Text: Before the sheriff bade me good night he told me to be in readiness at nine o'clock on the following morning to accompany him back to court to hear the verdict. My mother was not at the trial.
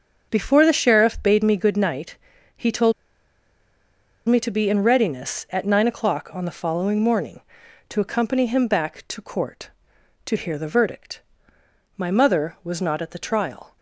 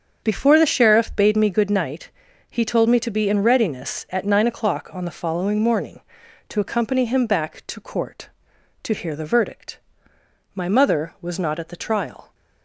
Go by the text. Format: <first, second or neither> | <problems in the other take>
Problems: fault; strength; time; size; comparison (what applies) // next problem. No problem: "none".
second | starts louder than the rest; strong; until 1.3 s; 7 dB; strong in the second // pauses between "night" and "he"; at 2.1 s; 0.40 s long; also in the second // pauses between "told" and "me"; strong; at 2.9 s; 1.3 s long